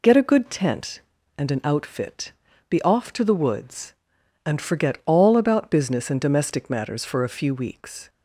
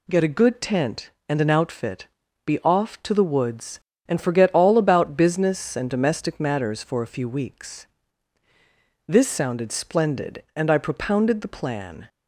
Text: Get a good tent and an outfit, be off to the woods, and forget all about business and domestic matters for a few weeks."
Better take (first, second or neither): first